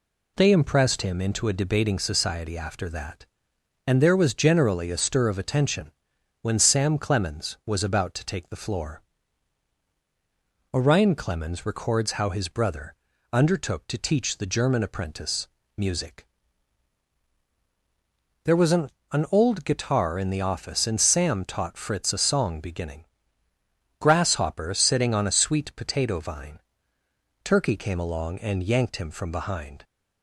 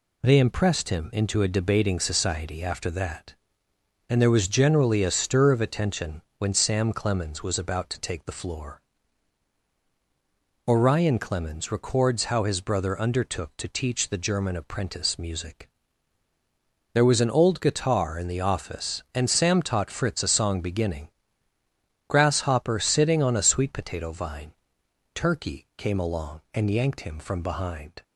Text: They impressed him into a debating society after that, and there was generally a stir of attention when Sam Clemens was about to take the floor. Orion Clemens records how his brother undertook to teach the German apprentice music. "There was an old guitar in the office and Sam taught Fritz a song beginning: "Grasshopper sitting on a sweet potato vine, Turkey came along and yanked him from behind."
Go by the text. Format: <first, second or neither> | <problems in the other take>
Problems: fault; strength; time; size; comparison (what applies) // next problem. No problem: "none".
second | pauses between "attention" and "when"; noticeable; at 5.9 s; 0.50 s long; slight in the second // pauses between "brother" and "undertook"; at 12.9 s; 0.40 s long // pauses between "apprentice" and "music"; slight; at 15.4 s; 0.28 s long // says "an" twice; at 19.1 s